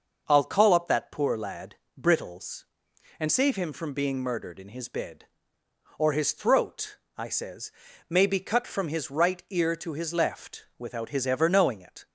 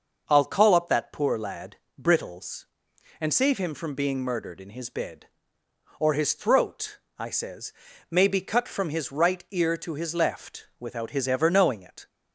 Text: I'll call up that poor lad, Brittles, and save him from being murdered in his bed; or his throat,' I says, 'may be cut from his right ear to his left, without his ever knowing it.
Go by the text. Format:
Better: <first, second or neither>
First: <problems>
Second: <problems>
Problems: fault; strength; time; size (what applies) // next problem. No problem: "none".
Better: neither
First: none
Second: none